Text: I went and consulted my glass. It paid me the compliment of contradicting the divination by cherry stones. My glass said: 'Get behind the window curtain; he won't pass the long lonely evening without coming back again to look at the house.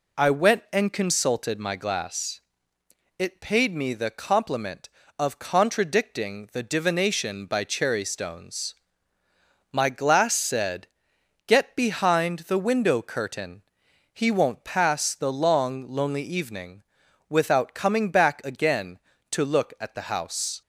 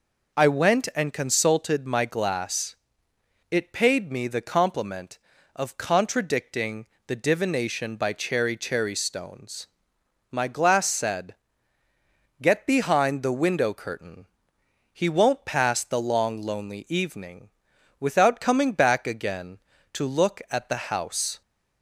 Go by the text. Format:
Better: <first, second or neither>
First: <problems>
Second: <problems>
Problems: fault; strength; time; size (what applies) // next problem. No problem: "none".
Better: first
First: pauses between "evening" and "without"; noticeable; at 16.8 s; 0.46 s long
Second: pauses between "contradicting" and "the"; slight; at 6.8 s; 0.18 s long // says "cherry" twice; at 8.5 s // pauses between "evening" and "without"; noticeable; at 17.5 s; 0.48 s long